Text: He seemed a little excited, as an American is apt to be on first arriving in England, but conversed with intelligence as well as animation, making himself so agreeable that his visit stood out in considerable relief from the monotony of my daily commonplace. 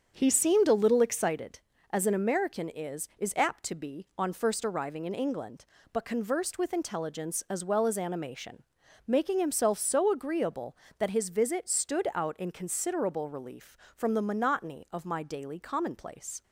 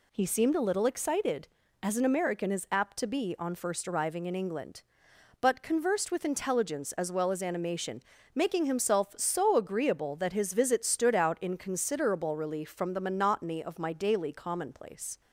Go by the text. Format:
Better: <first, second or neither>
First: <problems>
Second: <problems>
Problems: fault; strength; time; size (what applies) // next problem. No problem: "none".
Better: second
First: starts louder than the rest; strong; until 1.1 s; 7 dB // says "is" twice; at 3.1 s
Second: none